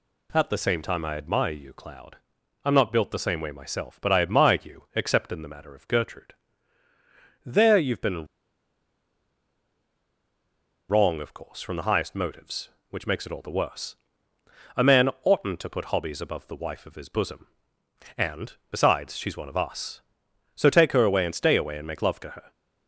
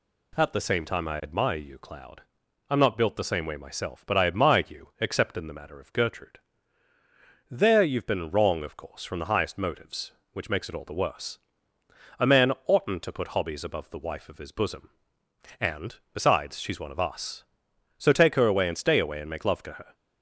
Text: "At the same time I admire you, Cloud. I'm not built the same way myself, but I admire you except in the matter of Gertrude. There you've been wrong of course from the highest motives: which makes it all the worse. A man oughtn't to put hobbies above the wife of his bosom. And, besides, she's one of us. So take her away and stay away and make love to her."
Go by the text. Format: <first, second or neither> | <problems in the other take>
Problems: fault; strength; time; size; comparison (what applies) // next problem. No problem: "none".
second | pauses between "been" and "wrong"; strong; at 8.2 s; 2.6 s long